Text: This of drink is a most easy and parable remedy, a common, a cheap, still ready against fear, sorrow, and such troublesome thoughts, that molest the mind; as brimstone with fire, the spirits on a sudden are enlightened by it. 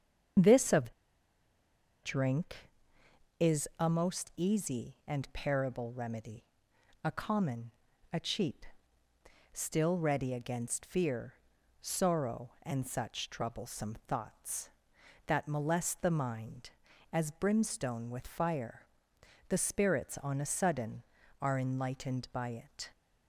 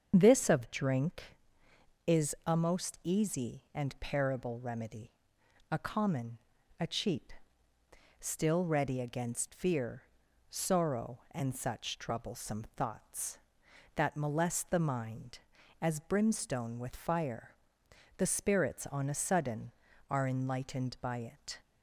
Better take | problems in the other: second | starts louder than the rest; until 2.5 s; 7 dB; also in the second // pauses between "of" and "drink"; at 0.9 s; 1.1 s long

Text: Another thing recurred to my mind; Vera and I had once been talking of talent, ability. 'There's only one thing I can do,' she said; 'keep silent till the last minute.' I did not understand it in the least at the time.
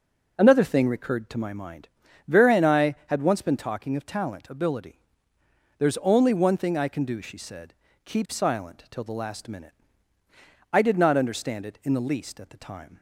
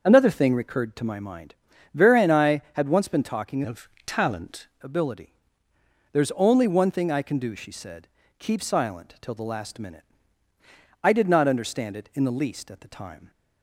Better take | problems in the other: first | changes voice from "of" to "talent"; from 3.6 to 4.6 s; 1.0 s long // pauses between "of" and "talent"; slight; at 3.8 s; 0.18 s long

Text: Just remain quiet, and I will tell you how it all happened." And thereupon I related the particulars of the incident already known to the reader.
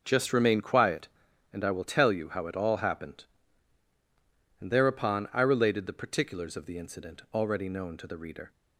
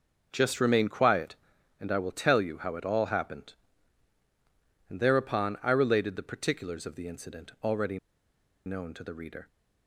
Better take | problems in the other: first | starts louder than the rest; noticeable; until 1.3 s; 6 dB; also in the first // pauses between "already" and "known"; noticeable; at 7.9 s; 0.68 s long

